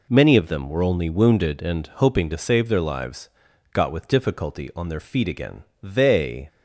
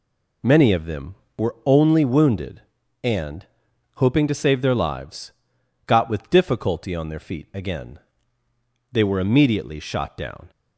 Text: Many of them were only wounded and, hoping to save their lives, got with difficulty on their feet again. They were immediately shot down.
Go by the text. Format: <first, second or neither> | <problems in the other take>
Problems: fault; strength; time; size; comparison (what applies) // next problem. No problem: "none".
second | stops before "were immediately shot down"; at 6.4 s